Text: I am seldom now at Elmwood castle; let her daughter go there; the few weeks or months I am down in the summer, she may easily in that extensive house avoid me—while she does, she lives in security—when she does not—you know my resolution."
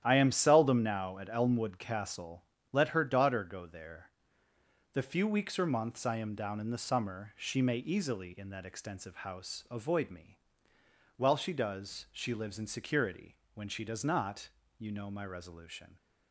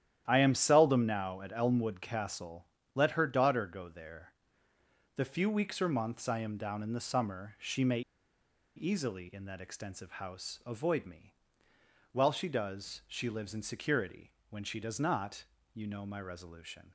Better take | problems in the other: first | starts louder than the rest; strong; until 1.2 s; 11 dB; strong in the first // pauses between "may" and "easily"; noticeable; at 8.0 s; 0.75 s long

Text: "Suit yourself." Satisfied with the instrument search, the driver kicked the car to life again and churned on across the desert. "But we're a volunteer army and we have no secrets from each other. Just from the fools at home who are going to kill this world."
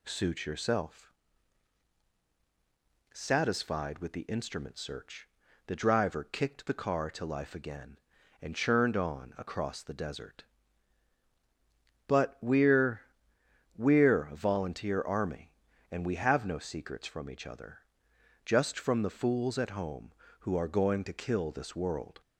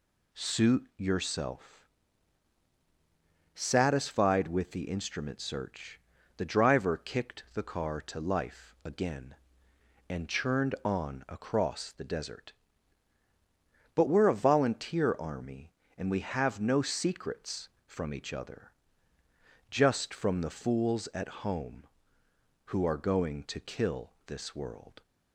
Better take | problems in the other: second | says "we're" twice; at 13.7 s

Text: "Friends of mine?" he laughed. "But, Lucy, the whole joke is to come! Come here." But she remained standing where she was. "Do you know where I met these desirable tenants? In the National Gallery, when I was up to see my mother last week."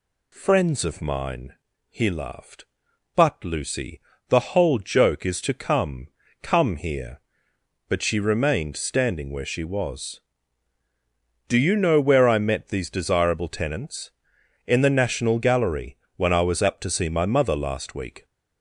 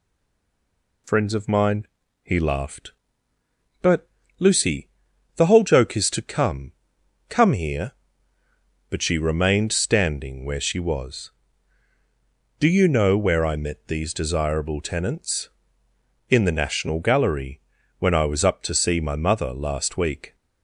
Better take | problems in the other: first | stays silent before the first word; until 1.0 s; 1.0 s long

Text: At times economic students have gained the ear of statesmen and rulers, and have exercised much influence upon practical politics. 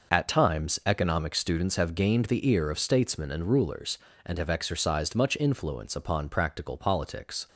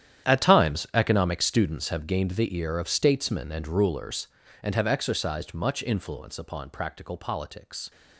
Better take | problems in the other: first | gets quieter; strong; throughout; 14.5 dB

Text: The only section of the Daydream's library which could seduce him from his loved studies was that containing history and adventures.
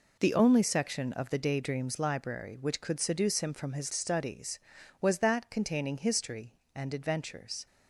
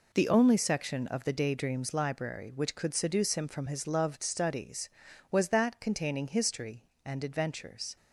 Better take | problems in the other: second | skips "loved"; at 3.9 s

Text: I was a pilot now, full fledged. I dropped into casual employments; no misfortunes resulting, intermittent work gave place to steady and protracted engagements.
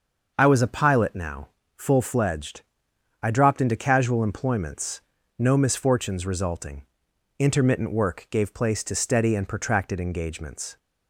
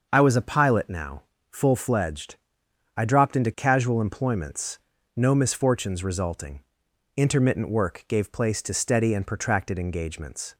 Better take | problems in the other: neither | starts louder than the rest; the same in both

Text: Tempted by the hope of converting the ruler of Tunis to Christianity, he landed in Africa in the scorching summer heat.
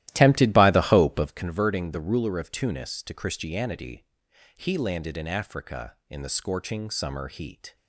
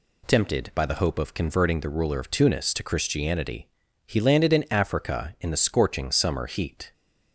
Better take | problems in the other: second | starts louder than the rest; strong; until 1.4 s; 14.5 dB

